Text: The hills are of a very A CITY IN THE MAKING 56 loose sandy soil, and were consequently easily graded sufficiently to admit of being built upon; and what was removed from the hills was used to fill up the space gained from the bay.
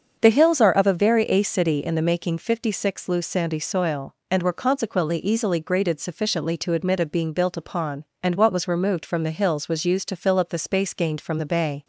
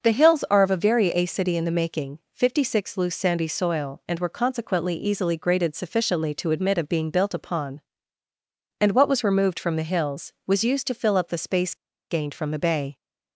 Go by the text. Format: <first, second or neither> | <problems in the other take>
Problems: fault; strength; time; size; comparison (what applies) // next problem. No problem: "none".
first | starts louder than the rest; until 1.0 s; 6 dB; also in the first // pauses between "space" and "gained"; slight; at 11.7 s; 0.35 s long